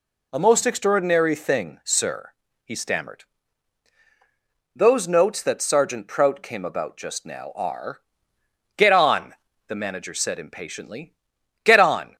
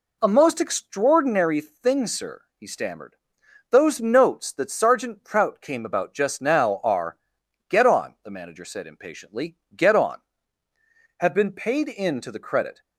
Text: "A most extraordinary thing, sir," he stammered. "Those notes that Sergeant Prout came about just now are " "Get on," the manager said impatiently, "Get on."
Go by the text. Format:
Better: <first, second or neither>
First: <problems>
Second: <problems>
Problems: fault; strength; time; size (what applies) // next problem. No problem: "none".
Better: first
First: none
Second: goes on to say "Have been paid in to the credit"; from 11.1 s on; 1.6 s long